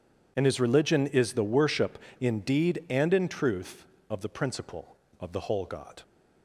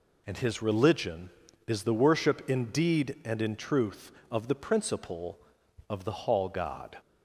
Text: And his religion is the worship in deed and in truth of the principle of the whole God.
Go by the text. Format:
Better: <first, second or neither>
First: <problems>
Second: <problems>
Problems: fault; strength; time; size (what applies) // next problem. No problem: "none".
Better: first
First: none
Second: says "hall" for "whole"; at 6.1 s